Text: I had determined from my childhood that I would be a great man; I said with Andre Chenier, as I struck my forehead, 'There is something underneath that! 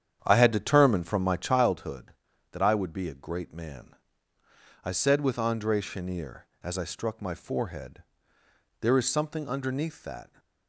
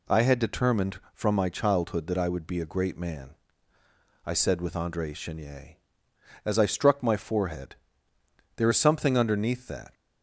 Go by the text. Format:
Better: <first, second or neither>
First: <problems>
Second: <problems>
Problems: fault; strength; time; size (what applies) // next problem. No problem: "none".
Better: second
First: starts louder than the rest; strong; until 1.8 s; 9 dB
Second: none